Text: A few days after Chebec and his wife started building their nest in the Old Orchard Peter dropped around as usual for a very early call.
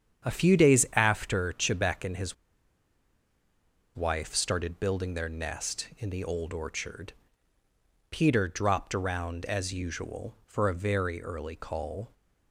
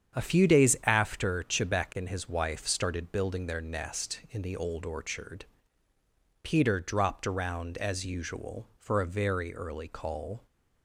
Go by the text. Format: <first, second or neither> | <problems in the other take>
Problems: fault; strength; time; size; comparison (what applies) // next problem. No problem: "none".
second | starts louder than the rest; strong; until 1.3 s; 8 dB; strong in the second // pauses between "his" and "wife"; strong; at 2.3 s; 1.6 s long // pauses between "Orchard" and "Peter"; noticeable; at 7.1 s; 0.98 s long; noticeable in the second